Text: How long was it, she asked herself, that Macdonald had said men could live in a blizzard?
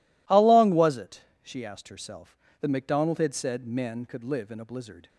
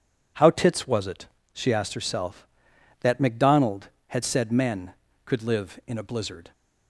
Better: first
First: none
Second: says "tits" for "long"; at 0.5 s

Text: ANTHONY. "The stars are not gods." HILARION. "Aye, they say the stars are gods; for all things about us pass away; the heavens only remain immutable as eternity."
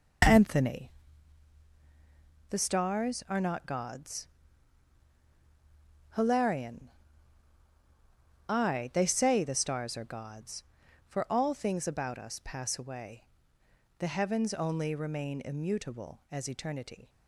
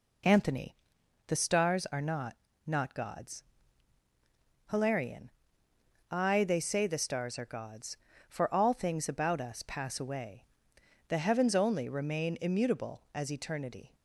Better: first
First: none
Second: says "not" twice; at 2.6 s

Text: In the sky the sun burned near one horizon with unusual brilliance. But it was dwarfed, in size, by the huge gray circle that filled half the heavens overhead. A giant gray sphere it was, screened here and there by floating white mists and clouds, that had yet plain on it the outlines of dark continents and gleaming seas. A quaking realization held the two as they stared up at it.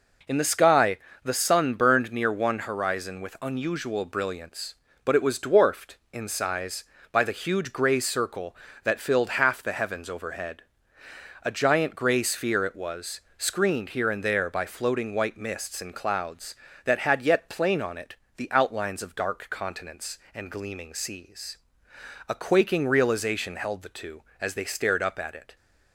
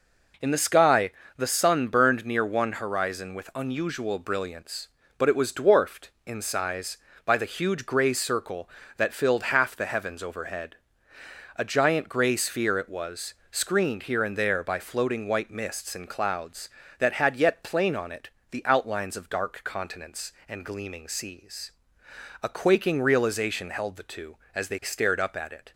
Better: neither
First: pauses between "sky" and "the"; slight; at 0.9 s; 0.26 s long // pauses between "it" and "the"; slight; at 18.1 s; 0.22 s long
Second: pauses between "sky" and "the"; slight; at 1.1 s; 0.26 s long // pauses between "it" and "the"; slight; at 18.2 s; 0.22 s long

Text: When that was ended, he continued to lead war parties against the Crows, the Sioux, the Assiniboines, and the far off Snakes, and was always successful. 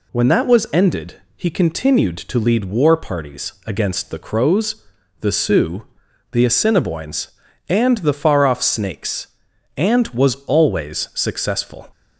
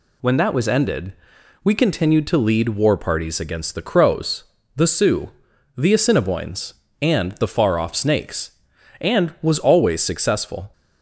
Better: first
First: none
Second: says "we" for "he"; at 1.6 s

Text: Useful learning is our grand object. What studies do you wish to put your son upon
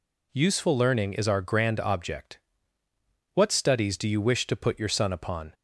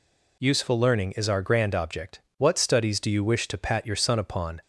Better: first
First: none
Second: says "pat" for "put"; at 3.5 s

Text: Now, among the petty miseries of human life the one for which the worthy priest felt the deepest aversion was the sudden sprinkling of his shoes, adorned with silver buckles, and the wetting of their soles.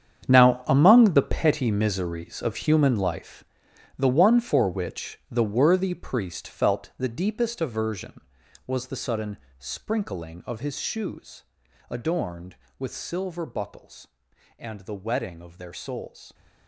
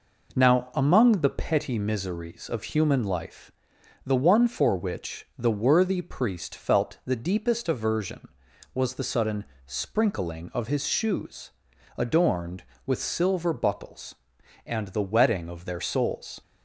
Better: second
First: gets quieter; strong; throughout; 13.5 dB // pauses between "life" and "the"; noticeable; at 3.4 s; 0.52 s long // pauses between "sudden" and "sprinkling"; slight; at 9.3 s; 0.22 s long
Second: pauses between "life" and "the"; noticeable; at 3.5 s; 0.52 s long // pauses between "sudden" and "sprinkling"; slight; at 9.4 s; 0.22 s long

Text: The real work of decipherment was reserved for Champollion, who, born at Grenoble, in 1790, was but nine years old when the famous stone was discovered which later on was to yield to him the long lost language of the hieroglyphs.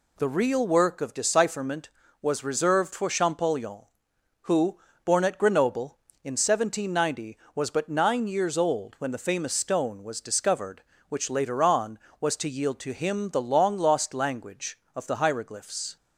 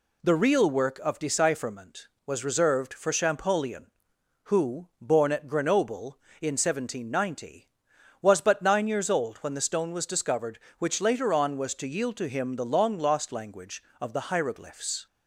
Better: first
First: none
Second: skips "famous"; at 9.6 s

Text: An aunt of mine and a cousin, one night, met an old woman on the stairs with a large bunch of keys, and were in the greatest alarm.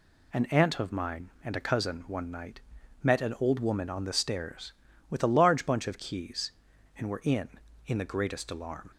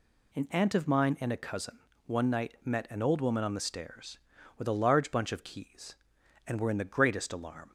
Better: second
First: says "in" twice; at 7.8 s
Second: none

